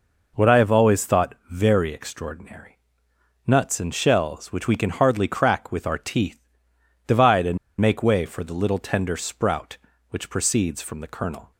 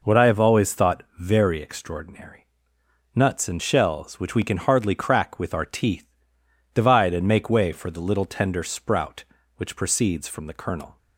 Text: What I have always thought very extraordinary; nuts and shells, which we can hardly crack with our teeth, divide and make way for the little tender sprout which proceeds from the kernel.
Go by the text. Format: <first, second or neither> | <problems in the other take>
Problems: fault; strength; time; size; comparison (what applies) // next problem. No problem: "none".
second | pauses between "and" and "make"; slight; at 7.5 s; 0.23 s long